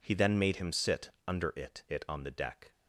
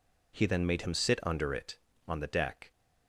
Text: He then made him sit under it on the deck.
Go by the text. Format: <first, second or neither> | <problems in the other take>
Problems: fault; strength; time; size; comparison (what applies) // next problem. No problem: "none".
second | pauses between "sit" and "under"; slight; at 1.1 s; 0.16 s long // says "it" twice; at 1.8 s